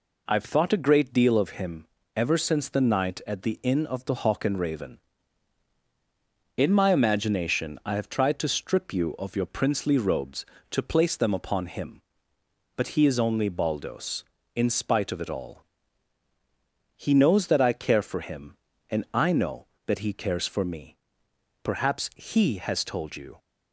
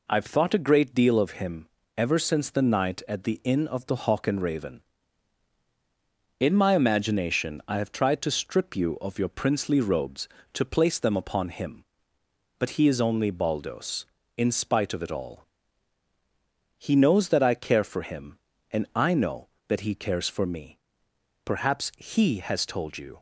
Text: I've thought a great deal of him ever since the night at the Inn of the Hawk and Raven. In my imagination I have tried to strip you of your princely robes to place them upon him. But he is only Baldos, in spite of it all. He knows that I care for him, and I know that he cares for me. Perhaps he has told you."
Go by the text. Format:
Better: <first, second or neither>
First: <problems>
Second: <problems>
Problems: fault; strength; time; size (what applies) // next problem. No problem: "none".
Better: neither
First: pauses between "him" and "ever"; slight; at 1.8 s; 0.30 s long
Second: pauses between "him" and "ever"; slight; at 1.6 s; 0.30 s long